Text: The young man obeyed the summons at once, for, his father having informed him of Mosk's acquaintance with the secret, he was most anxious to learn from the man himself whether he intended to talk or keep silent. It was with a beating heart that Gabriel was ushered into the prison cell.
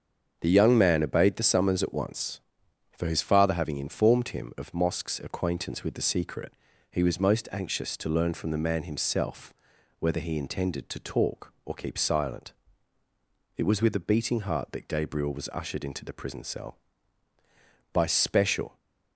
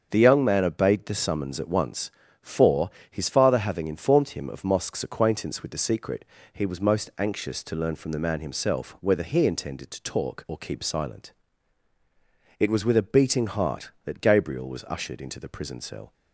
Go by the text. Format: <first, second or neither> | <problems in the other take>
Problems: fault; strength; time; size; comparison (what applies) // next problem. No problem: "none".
second | starts louder than the rest; until 1.4 s; 7 dB; strong in the second // pauses between "himself" and "whether"; noticeable; at 9.5 s; 0.46 s long // goes on to say "By special"; noticeable; from 17.9 s on; 0.84 s long